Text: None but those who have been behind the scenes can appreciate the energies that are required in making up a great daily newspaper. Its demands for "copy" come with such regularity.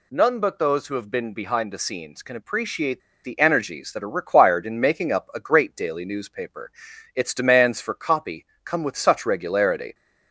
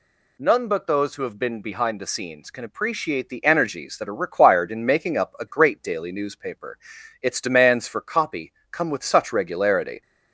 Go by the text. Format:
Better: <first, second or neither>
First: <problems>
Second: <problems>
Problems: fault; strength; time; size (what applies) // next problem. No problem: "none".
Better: second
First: pauses between "appreciate" and "the"; slight; at 3.0 s; 0.23 s long // pauses between "copy" and "come"; slight; at 8.4 s; 0.18 s long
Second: pauses between "copy" and "come"; slight; at 8.5 s; 0.18 s long